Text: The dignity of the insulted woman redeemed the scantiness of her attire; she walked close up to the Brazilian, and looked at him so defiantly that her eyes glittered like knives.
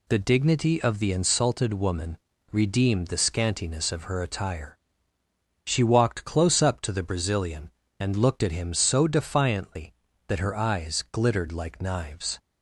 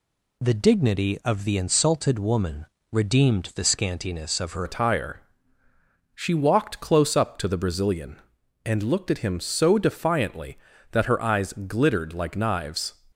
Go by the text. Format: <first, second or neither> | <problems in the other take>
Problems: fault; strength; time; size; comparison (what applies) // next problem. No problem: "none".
first | pauses between "woman" and "redeemed"; slight; at 2.6 s; 0.26 s long; slight in the first // changes voice at "attire"; from 4.6 s on; 8.3 s long